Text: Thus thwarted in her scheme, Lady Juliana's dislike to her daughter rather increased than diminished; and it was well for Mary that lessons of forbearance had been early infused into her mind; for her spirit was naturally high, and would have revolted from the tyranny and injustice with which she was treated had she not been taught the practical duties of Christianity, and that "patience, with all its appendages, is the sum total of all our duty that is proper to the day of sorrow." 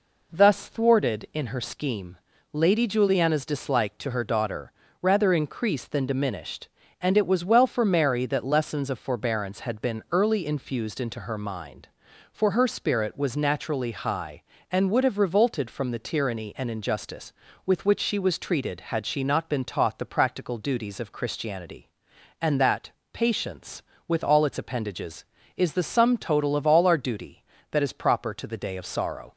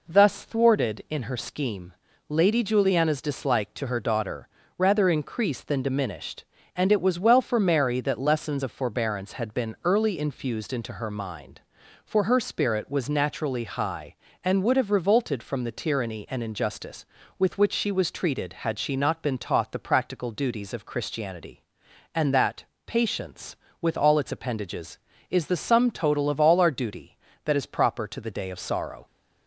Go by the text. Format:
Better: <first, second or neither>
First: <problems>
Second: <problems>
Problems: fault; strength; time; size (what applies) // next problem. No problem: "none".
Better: neither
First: pauses between "daughter" and "rather"; slight; at 4.7 s; 0.30 s long // pauses between "that" and "patience"; slight; at 22.8 s; 0.24 s long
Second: pauses between "daughter" and "rather"; slight; at 4.4 s; 0.30 s long // pauses between "that" and "patience"; slight; at 22.6 s; 0.24 s long